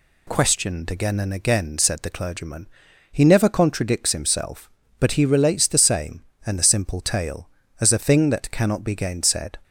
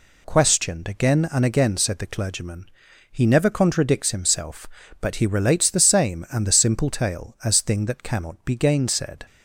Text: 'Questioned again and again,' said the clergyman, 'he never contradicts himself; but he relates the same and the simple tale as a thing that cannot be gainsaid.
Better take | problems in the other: first | skips "a"; at 7.6 s

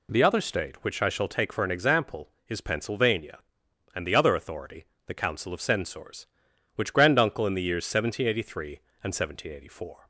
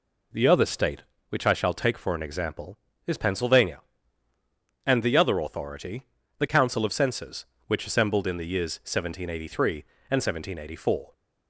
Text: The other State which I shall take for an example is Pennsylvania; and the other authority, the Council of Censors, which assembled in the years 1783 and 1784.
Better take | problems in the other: second | says "granduncle" for "assembled"; at 6.9 s

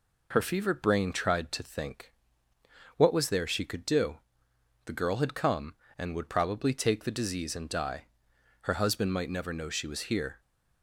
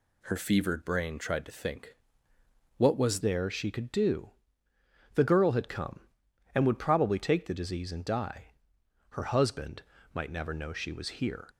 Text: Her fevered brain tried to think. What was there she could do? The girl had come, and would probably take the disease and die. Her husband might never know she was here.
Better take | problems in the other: first | changes voice at "there"; from 3.2 s on; 8.2 s long // pauses between "husband" and "might"; slight; at 9.8 s; 0.32 s long

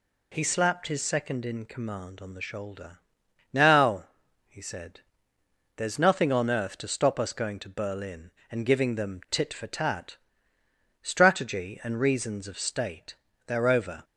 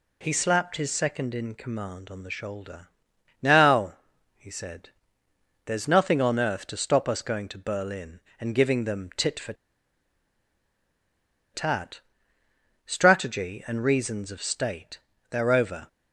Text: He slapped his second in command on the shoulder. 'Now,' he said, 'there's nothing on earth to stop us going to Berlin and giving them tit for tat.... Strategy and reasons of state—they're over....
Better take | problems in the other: first | pauses between "for" and "tat"; strong; at 9.5 s; 2.0 s long

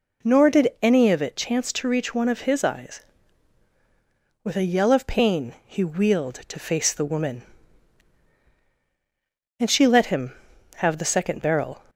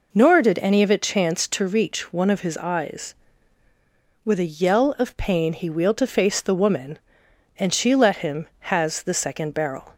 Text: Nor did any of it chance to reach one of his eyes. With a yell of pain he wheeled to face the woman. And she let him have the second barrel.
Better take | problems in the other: first | says "has" for "have"; at 8.6 s

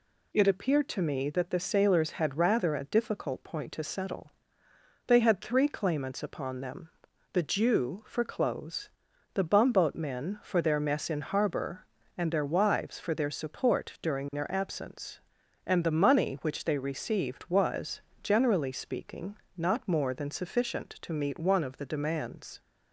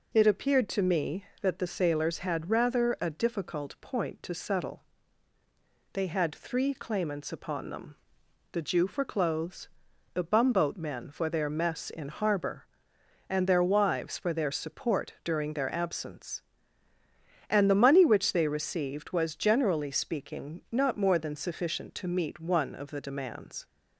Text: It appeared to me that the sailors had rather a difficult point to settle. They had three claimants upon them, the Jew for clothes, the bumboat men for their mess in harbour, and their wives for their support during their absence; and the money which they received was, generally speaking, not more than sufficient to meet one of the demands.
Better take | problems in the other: neither | none

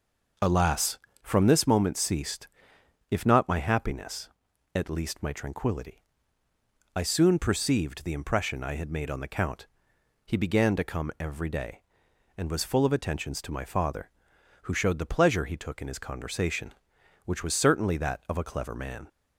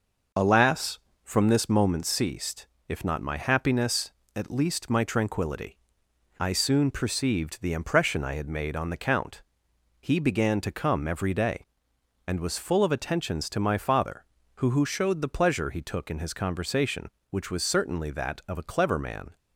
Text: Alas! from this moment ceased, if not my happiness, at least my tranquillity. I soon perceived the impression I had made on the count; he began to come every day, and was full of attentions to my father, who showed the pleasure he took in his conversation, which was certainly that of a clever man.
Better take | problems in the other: first | says "who" twice; at 14.6 s

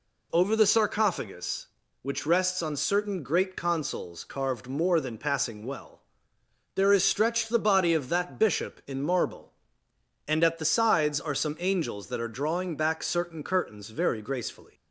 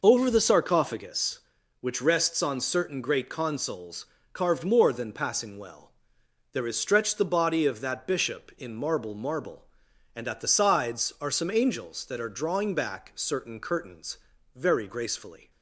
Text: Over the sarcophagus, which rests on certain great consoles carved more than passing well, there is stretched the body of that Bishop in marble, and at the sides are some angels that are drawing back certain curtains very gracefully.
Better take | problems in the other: first | pauses between "consoles" and "carved"; slight; at 4.0 s; 0.26 s long // says "marble" twice; at 9.1 s // pauses between "curtains" and "very"; slight; at 14.1 s; 0.36 s long

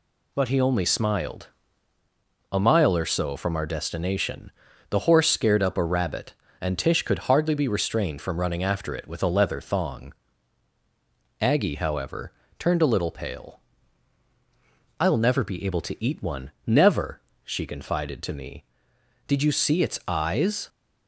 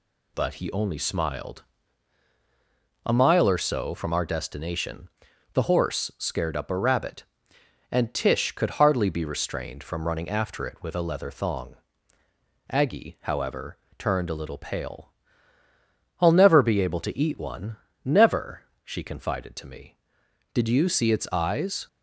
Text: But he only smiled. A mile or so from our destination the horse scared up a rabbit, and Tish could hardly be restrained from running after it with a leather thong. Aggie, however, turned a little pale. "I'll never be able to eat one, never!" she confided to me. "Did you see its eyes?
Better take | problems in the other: neither | pauses between "destination" and "the"; the same in both

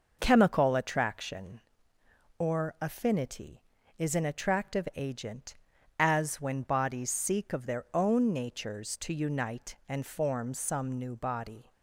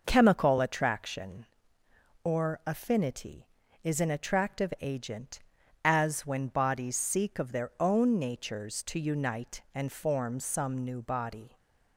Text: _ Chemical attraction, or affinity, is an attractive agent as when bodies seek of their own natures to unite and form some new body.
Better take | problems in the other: neither | none

